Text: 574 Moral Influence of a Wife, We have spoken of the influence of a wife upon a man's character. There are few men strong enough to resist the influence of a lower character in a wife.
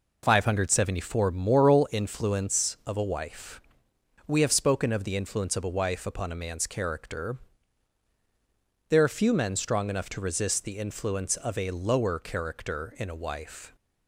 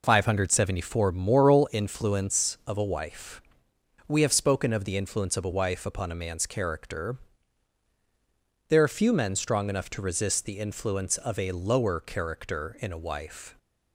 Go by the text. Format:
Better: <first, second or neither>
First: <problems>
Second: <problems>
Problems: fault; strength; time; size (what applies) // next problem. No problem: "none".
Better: neither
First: none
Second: none